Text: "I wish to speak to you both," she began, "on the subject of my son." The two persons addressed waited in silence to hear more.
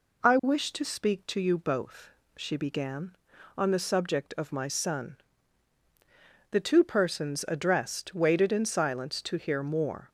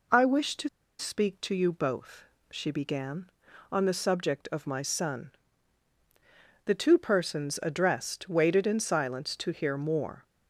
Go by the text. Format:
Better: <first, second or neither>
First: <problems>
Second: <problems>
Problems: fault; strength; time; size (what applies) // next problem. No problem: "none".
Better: first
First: none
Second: pauses between "to" and "speak"; slight; at 0.6 s; 0.30 s long